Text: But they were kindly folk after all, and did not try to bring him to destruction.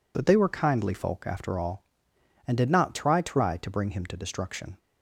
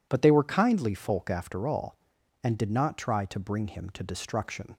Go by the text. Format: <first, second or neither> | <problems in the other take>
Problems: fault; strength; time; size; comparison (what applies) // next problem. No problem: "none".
second | says "try" twice; at 3.1 s